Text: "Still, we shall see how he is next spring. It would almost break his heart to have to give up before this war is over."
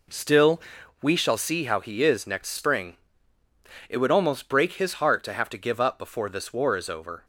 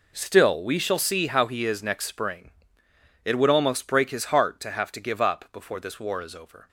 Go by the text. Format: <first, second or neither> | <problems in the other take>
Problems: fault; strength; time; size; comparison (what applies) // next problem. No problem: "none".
neither | none